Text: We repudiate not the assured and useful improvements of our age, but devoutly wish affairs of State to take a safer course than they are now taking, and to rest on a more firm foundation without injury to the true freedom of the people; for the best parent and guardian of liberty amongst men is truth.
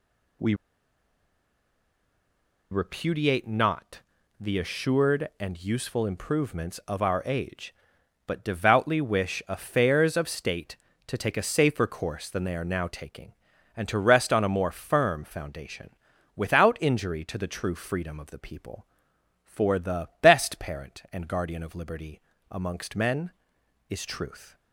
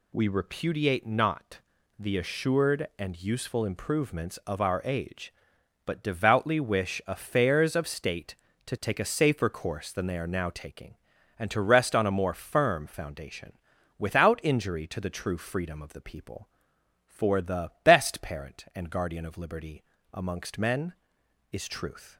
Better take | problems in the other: second | pauses between "We" and "repudiate"; strong; at 0.5 s; 2.1 s long // pauses between "not" and "the"; at 4.0 s; 0.38 s long; also in the second // pauses between "foundation" and "without"; noticeable; at 15.9 s; 0.46 s long; noticeable in the second // pauses between "liberty" and "amongst"; slight; at 22.2 s; 0.30 s long; slight in the second

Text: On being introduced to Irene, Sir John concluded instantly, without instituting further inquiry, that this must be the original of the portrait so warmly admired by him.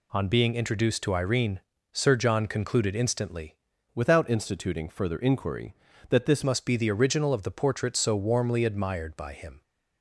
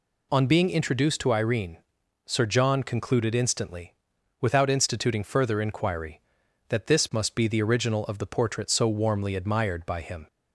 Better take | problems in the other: second | changes voice from "without" to "this"; from 3.9 to 6.4 s; 2.5 s long

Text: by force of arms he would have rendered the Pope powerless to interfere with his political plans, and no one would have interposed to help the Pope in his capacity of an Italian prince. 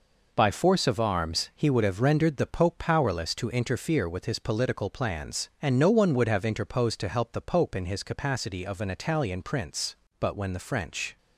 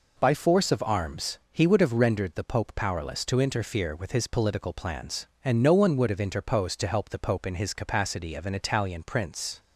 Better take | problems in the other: second | goes on to say "But when the French"; noticeable; from 10.1 s on; 0.98 s long

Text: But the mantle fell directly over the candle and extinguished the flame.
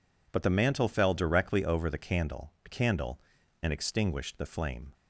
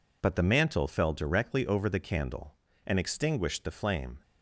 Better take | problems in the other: second | says "candle" twice; at 2.6 s

